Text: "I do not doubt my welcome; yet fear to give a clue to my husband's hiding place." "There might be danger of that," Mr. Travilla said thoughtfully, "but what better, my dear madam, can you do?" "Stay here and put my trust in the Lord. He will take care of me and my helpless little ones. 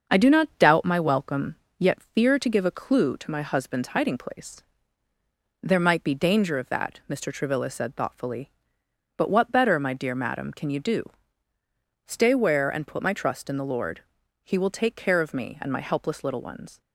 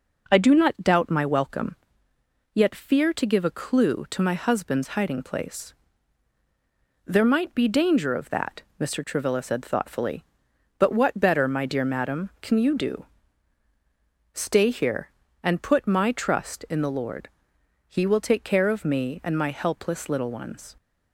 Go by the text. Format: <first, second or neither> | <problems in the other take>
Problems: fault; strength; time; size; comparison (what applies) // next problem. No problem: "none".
second | starts louder than the rest; until 1.1 s; 6.5 dB // says "where" for "here"; at 12.3 s